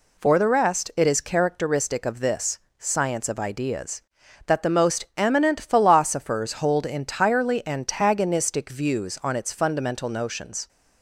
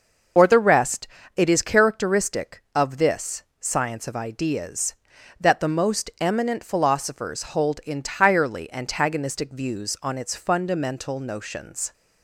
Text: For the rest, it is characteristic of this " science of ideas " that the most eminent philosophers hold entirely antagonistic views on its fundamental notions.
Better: first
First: none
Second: loses the start of "For"; at 0.3 s; 85 ms // starts louder than the rest; noticeable; until 1.6 s; 6 dB

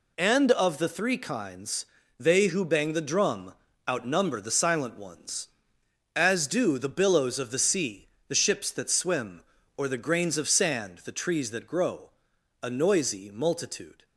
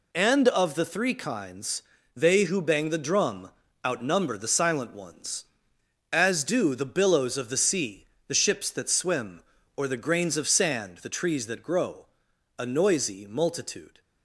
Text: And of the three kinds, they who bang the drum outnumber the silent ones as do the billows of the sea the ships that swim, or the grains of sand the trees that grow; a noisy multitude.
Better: neither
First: pauses between "drum" and "outnumber"; slight; at 3.5 s; 0.36 s long // pauses between "sea" and "the"; slight; at 8.0 s; 0.21 s long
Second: pauses between "drum" and "outnumber"; slight; at 3.4 s; 0.36 s long // pauses between "sea" and "the"; slight; at 8.0 s; 0.22 s long

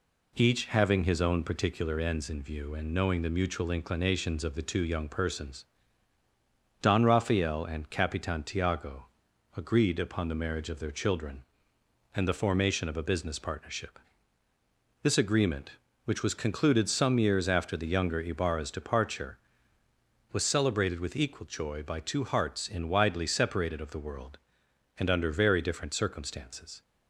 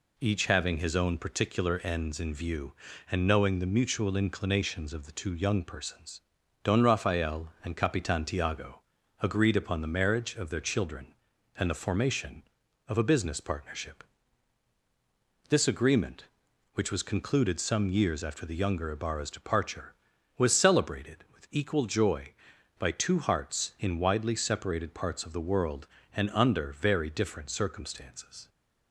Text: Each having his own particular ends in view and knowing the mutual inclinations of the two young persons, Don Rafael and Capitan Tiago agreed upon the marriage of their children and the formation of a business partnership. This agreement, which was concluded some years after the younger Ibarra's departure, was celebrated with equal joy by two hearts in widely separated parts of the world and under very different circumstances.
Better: second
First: pauses between "Tiago" and "agreed"; noticeable; at 9.0 s; 0.50 s long // skips "parts"; at 23.8 s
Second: pauses between "Tiago" and "agreed"; at 8.8 s; 0.40 s long

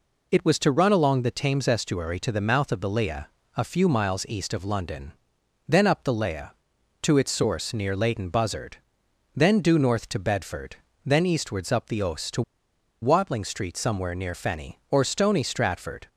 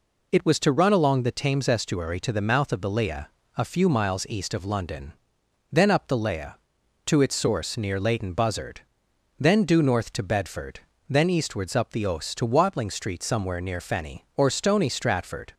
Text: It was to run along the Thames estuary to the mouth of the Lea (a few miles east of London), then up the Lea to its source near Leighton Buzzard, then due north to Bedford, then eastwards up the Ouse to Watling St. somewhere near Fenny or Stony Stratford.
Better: second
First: pauses between "to" and "Watling"; noticeable; at 12.4 s; 0.60 s long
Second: none

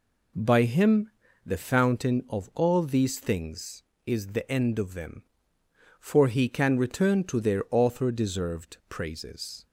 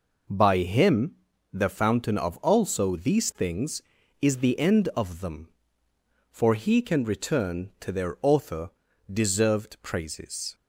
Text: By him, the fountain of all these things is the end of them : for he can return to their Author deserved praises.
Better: first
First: none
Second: says "also" for "all"; at 2.3 s // pauses between "Author" and "deserved"; at 8.7 s; 0.42 s long

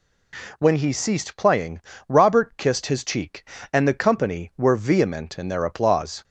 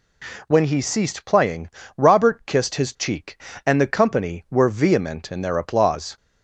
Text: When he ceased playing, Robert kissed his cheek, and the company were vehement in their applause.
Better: neither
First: none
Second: none

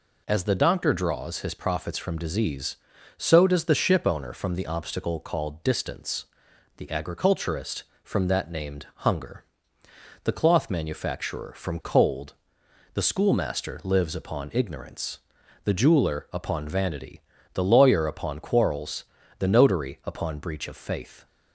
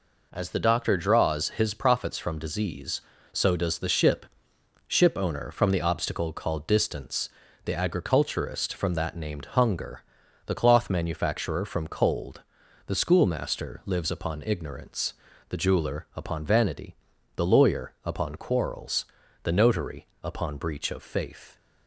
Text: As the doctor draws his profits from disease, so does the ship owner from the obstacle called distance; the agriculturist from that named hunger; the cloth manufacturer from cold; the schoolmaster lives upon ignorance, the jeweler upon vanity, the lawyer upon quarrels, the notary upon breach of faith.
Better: first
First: none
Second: says "ship" twice; at 4.8 s // pauses between "notary" and "upon"; slight; at 20.0 s; 0.18 s long

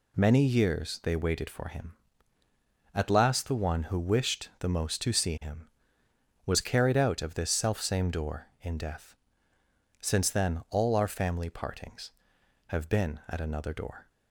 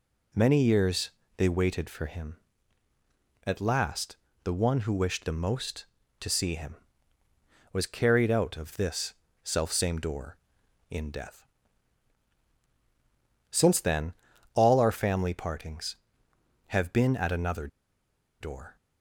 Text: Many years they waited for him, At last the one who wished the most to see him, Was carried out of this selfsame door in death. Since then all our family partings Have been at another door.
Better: first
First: none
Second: pauses between "years" and "they"; slight; at 1.1 s; 0.26 s long // pauses between "last" and "the"; slight; at 4.1 s; 0.28 s long // pauses between "this" and "selfsame"; slight; at 9.1 s; 0.30 s long // pauses between "then" and "all"; at 14.1 s; 0.42 s long // pauses between "another" and "door"; noticeable; at 17.6 s; 0.73 s long

